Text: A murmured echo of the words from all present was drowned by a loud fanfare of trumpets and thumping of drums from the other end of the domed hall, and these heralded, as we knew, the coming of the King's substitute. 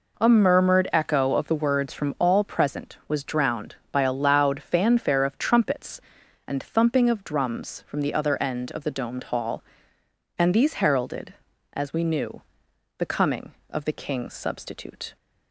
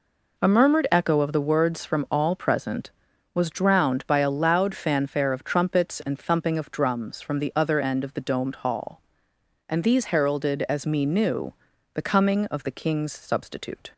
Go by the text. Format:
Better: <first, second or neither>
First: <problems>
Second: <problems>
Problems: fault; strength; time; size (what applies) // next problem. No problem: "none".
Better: first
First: none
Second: says "me" for "we"; at 10.8 s